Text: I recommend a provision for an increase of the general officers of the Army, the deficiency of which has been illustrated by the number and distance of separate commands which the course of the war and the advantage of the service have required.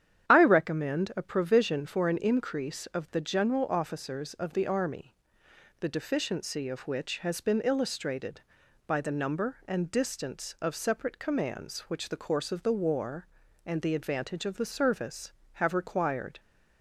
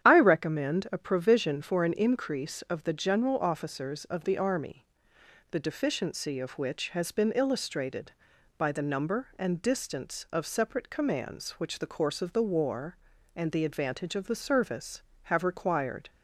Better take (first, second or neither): neither